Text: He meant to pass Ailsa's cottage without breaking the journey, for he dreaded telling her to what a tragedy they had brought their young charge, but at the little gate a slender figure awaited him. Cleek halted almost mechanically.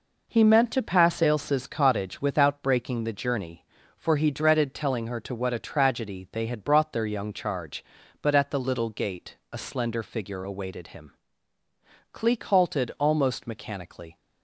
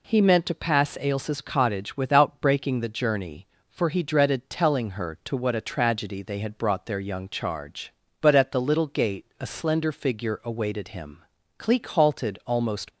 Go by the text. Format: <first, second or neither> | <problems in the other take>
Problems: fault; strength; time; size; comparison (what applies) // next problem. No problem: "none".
first | pauses between "gate" and "a"; slight; at 9.2 s; 0.16 s long; slight in the first // stops before "mechanically"; at 12.9 s